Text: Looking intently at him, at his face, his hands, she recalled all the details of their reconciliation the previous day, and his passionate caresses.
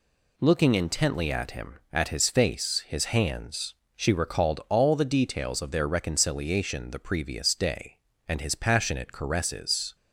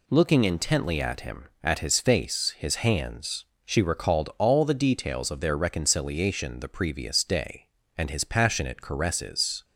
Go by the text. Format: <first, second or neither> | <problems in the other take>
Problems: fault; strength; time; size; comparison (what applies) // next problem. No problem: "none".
neither | none